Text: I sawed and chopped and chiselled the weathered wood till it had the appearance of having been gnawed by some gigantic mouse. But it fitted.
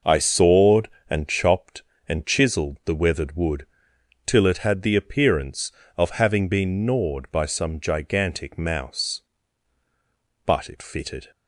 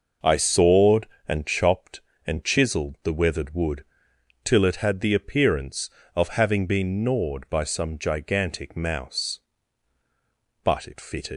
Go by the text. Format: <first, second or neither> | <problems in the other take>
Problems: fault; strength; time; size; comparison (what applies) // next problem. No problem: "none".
first | pauses between "wood" and "till"; noticeable; at 3.8 s; 0.60 s long; noticeable in the first // leaves "fitted" unfinished; at 11.3 s; 125 ms